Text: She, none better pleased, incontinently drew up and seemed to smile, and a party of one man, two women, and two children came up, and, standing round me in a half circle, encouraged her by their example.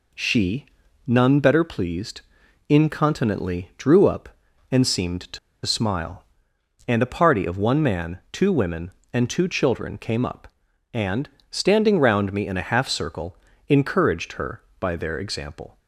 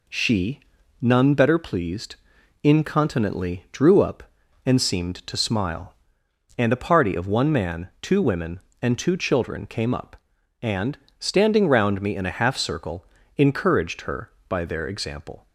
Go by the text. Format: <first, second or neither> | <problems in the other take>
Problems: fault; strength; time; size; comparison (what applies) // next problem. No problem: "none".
second | pauses between "to" and "smile"; slight; at 5.3 s; 0.27 s long